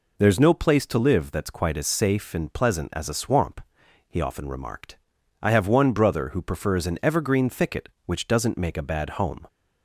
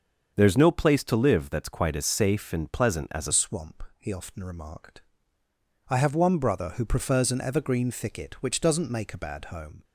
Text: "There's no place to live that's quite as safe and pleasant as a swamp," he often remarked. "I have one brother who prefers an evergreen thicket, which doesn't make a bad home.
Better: first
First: none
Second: starts louder than the rest; until 1.3 s; 7 dB // changes voice at "swamp"; from 3.3 s on; 6.5 s long

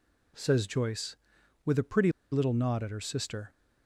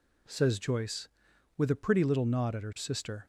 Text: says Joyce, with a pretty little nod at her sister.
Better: second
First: pauses between "pretty" and "little"; slight; at 2.1 s; 0.21 s long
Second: none

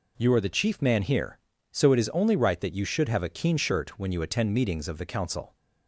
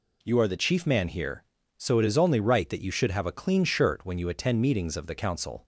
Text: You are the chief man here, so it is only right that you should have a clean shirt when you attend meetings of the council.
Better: second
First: says "keen" for "clean"; at 3.2 s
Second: none

